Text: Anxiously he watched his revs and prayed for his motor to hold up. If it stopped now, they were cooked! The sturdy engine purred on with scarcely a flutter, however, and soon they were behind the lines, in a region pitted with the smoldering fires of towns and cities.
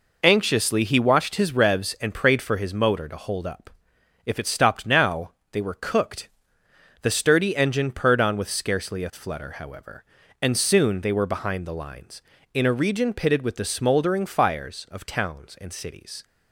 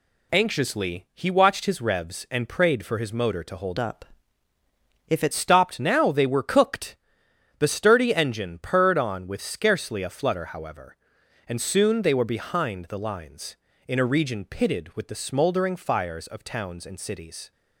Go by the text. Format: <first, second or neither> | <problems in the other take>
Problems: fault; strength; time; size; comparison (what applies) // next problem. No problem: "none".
first | changes voice from "up" to "it"; from 3.7 to 5.3 s; 1.6 s long